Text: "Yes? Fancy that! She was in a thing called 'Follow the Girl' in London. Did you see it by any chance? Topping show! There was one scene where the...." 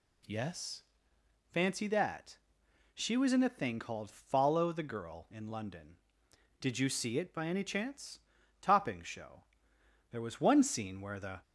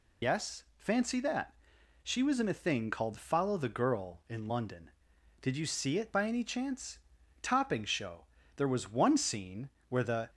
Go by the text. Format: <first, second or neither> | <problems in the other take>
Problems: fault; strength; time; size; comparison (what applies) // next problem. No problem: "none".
first | loses the start of "Yes"; at 0.2 s; 80 ms // pauses between "scene" and "where"; slight; at 9.6 s; 0.20 s long